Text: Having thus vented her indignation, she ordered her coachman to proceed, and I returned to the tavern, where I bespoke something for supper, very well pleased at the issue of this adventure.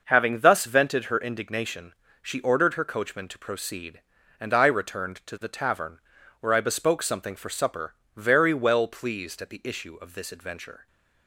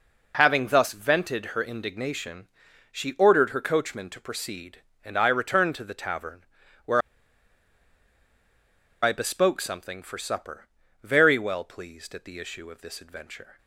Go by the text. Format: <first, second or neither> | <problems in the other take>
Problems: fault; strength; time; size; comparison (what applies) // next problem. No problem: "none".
first | pauses between "where" and "I"; strong; at 6.9 s; 2.0 s long